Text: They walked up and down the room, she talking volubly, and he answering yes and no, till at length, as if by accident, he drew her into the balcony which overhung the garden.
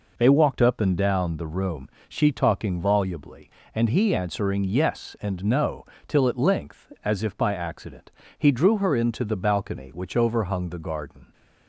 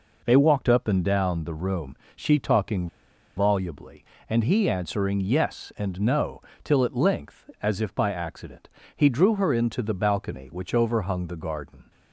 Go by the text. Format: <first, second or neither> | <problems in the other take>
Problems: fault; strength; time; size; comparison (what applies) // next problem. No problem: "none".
first | pauses between "talking" and "volubly"; noticeable; at 2.8 s; 0.49 s long